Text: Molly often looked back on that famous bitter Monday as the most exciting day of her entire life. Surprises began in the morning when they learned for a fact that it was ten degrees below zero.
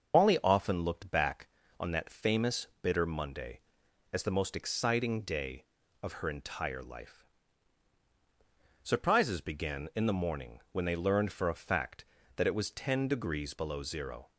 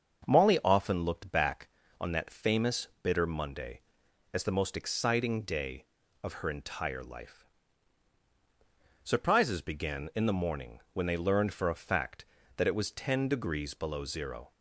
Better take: second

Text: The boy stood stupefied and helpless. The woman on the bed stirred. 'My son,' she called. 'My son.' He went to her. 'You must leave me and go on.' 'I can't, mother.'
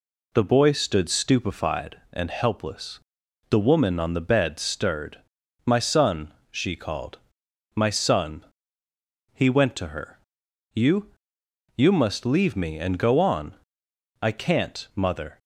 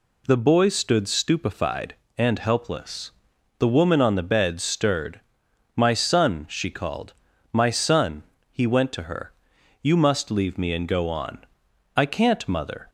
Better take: second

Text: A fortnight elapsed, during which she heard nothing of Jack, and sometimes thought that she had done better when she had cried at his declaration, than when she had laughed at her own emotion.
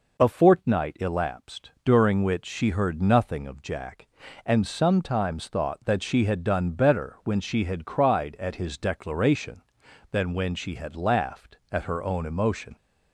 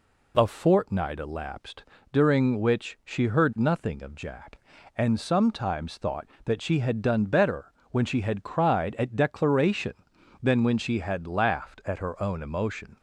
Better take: first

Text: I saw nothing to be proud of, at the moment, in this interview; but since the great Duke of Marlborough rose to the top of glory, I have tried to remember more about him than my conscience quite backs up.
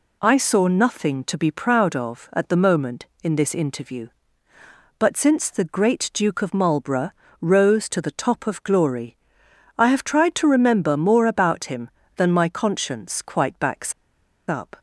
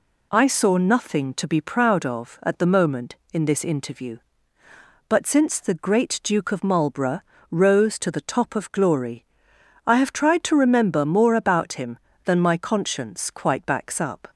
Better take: second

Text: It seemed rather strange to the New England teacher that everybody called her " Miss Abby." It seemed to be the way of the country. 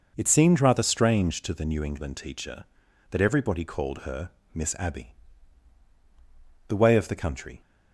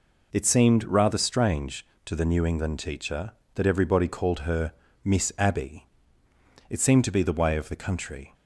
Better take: second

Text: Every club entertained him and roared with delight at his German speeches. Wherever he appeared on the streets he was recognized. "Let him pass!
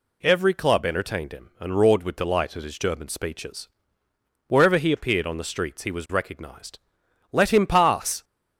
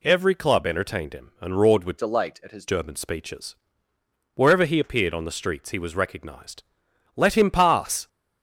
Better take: first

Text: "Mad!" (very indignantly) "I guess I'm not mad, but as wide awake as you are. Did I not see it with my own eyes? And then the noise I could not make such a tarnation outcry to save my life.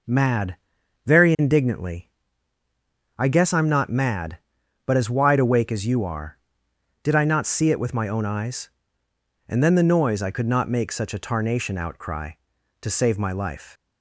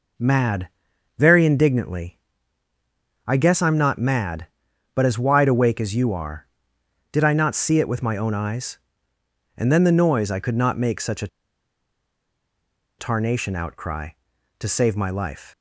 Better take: first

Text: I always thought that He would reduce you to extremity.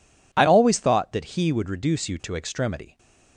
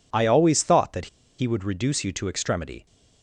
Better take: first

